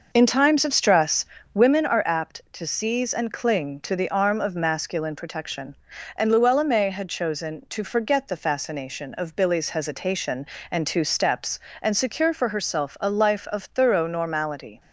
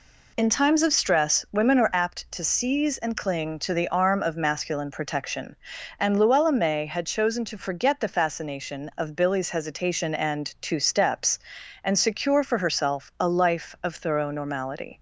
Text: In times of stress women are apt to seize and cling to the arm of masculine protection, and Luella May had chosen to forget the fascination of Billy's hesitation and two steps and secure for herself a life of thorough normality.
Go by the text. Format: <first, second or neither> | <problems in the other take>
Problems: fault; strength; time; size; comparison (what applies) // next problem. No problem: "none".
second | starts louder than the rest; noticeable; until 1.9 s; 5.5 dB // pauses between "stress" and "women"; slight; at 1.2 s; 0.28 s long